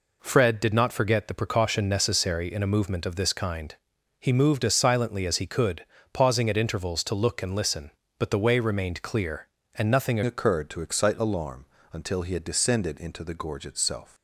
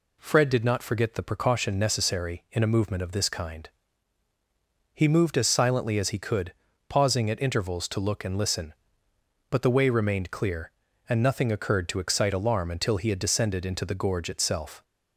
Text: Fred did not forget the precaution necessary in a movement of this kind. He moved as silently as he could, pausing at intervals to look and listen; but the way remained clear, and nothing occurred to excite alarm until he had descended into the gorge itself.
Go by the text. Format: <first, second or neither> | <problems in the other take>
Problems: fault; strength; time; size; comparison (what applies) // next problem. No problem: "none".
second | changes voice at "occurred"; from 10.2 s on; 3.9 s long // pauses between "alarm" and "until"; slight; at 11.6 s; 0.26 s long